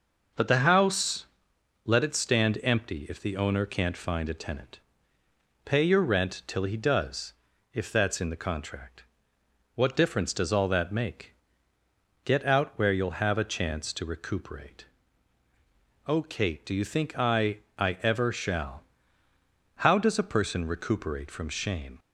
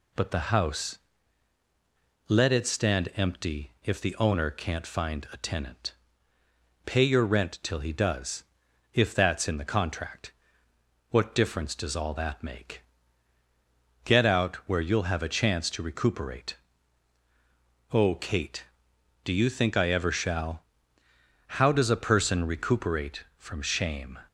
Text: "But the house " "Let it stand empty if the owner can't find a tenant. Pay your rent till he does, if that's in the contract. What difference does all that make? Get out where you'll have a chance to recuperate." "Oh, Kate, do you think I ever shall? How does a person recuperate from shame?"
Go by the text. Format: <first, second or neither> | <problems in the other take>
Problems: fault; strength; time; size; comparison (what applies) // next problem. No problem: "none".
second | says "I" twice; at 17.7 s